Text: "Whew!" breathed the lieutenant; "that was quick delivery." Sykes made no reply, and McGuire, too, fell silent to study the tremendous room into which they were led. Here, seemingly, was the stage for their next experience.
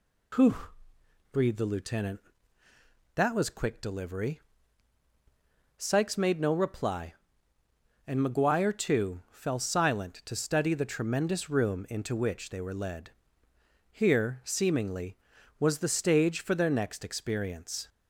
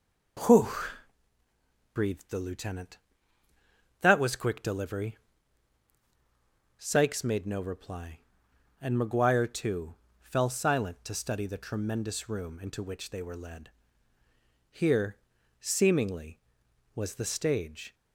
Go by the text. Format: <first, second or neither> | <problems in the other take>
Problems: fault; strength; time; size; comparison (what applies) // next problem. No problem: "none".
first | stops before "for their next experience"; at 17.9 s